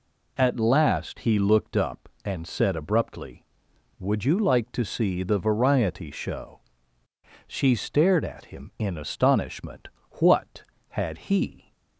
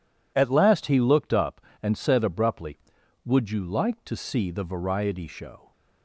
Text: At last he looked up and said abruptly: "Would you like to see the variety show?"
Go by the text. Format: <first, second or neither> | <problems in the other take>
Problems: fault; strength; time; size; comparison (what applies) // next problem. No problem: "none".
second | goes on to say "She stared at him in astonishment What had he"; strong; from 7.4 s on; 4.2 s long